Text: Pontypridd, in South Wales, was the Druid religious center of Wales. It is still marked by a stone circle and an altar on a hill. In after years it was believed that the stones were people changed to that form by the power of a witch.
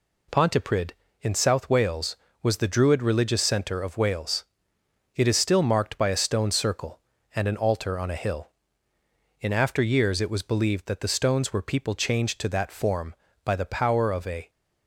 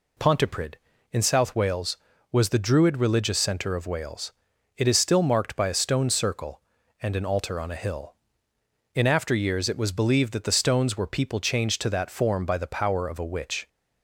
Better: second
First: stops before "witch"; at 14.4 s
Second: none

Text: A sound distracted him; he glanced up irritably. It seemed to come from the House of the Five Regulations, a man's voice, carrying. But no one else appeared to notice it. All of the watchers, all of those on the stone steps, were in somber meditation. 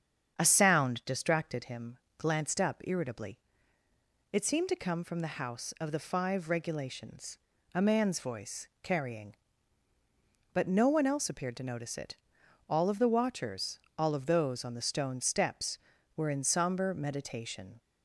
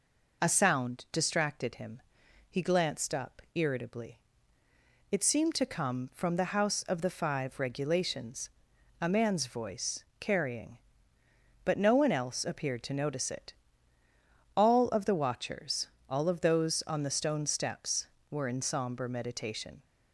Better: second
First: starts louder than the rest; strong; until 1.3 s; 7.5 dB // skips "he"; at 2.0 s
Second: none

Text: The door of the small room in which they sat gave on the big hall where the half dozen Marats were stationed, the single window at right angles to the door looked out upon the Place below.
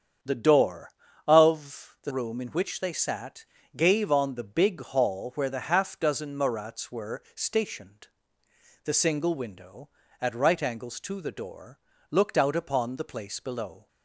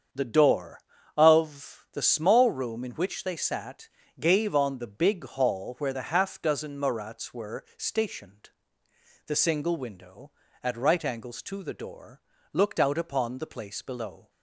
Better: second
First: starts louder than the rest; strong; until 1.6 s; 8 dB // skips "small"; at 2.1 s // pauses between "sat" and "gave"; slight; at 3.4 s; 0.32 s long // pauses between "door" and "looked"; slight; at 11.7 s; 0.32 s long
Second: starts louder than the rest; strong; until 1.5 s; 7.5 dB // pauses between "sat" and "gave"; slight; at 3.8 s; 0.32 s long // pauses between "door" and "looked"; slight; at 12.2 s; 0.32 s long

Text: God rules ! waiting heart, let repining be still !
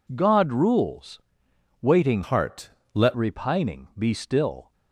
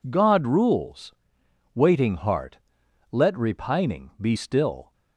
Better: second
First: changes voice from "heart" to "let"; from 2.2 to 3.1 s; 0.9 s long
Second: none

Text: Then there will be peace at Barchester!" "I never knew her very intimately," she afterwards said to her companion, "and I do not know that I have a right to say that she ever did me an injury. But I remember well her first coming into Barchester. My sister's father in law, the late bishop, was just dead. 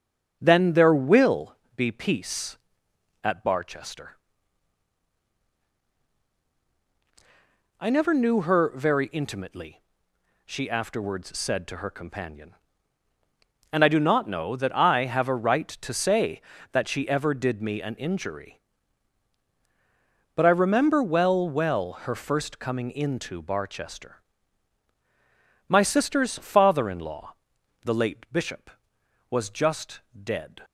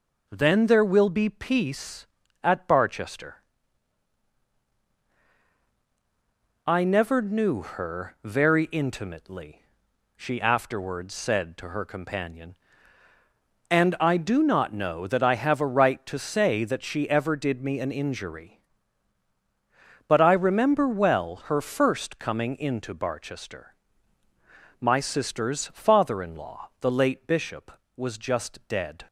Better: second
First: starts louder than the rest; until 1.4 s; 7 dB // pauses between "will" and "be"; slight; at 1.5 s; 0.20 s long // says "well" twice; at 21.4 s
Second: none

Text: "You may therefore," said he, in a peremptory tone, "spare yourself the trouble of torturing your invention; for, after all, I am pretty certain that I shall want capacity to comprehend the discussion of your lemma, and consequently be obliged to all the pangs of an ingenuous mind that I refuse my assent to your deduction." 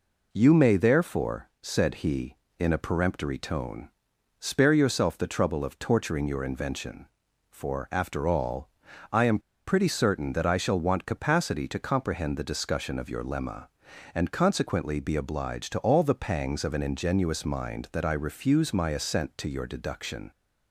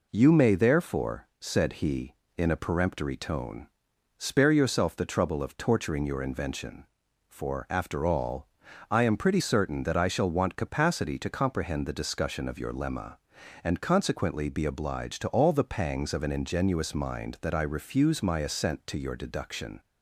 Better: second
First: pauses between "am" and "pretty"; slight; at 9.3 s; 0.28 s long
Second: none

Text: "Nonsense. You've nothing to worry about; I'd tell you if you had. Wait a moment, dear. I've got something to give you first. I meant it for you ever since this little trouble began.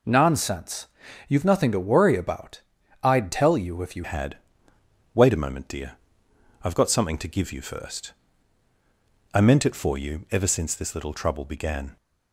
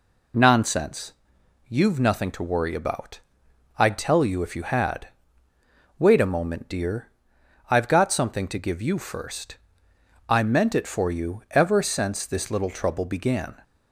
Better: second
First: changes voice at "had"; from 4.0 s on; 7.9 s long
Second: none

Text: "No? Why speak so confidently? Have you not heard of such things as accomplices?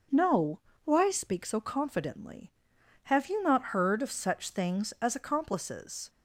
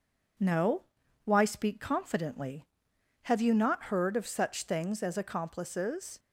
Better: first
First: none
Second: skips "so"; at 1.8 s

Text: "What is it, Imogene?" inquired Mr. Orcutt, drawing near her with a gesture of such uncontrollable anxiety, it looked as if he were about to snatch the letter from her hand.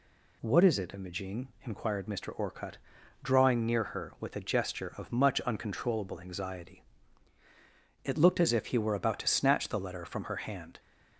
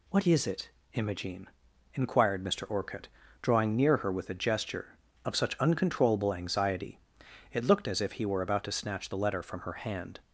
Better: second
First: says "much" for "such"; at 5.1 s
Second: none

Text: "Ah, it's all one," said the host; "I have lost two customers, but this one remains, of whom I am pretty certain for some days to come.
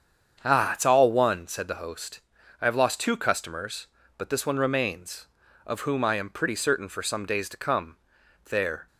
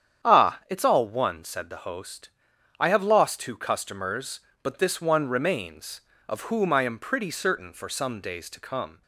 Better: second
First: starts louder than the rest; strong; until 1.4 s; 7.5 dB // goes on to say "There"; slight; from 8.4 s on; 0.42 s long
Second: starts louder than the rest; strong; until 1.3 s; 9 dB

